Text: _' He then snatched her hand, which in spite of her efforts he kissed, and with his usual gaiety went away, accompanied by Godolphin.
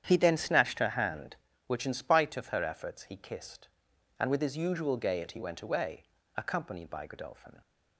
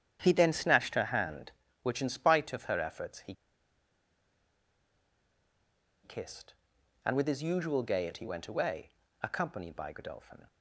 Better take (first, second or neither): first